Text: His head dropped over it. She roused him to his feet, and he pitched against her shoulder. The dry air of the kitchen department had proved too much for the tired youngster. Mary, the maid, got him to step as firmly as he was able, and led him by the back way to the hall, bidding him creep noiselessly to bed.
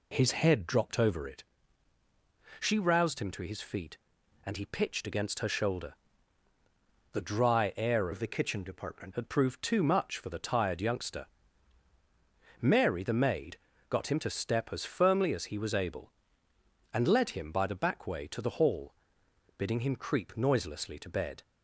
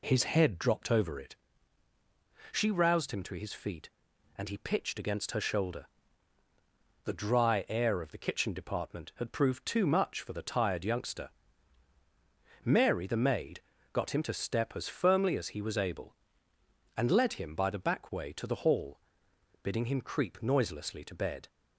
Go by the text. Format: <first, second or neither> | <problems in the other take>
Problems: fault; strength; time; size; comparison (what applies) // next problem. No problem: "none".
second | changes voice from "of" to "department"; from 8.1 to 9.1 s; 1.0 s long